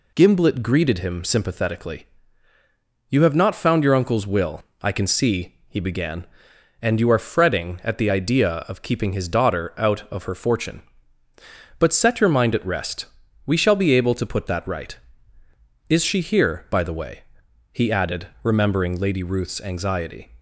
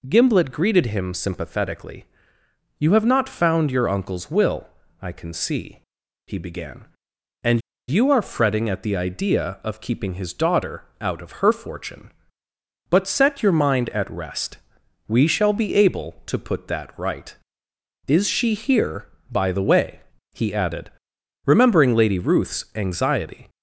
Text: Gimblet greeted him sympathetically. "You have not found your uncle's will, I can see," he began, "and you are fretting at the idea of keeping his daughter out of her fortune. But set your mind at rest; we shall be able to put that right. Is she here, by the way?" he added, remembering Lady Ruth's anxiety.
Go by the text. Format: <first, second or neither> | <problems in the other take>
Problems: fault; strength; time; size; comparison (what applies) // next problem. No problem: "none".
first | pauses between "and" and "you"; slight; at 7.6 s; 0.28 s long // pauses between "daughter" and "out"; slight; at 10.8 s; 0.18 s long